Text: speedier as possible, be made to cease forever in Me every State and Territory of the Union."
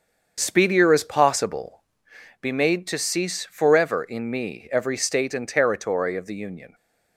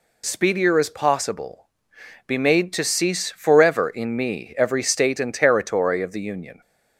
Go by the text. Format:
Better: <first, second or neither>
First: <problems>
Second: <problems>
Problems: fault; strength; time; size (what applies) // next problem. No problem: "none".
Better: second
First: starts louder than the rest; strong; until 2.1 s; 7 dB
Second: none